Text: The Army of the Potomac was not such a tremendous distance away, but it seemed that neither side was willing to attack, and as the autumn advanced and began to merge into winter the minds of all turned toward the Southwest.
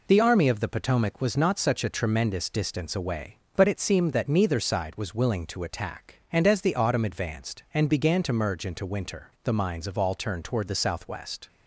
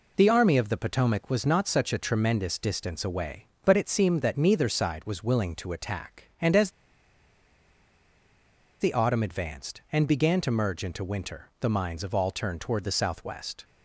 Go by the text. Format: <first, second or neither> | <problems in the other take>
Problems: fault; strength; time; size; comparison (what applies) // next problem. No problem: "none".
first | pauses between "as" and "the"; strong; at 6.7 s; 2.0 s long